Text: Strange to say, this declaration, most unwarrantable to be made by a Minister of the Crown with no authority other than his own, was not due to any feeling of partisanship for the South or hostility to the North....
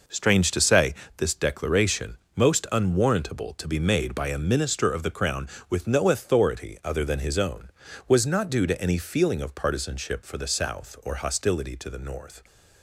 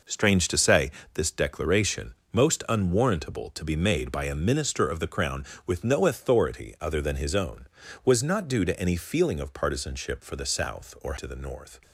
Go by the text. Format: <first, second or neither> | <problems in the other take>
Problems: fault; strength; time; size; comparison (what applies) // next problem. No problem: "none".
first | skips "hostility"; at 11.1 s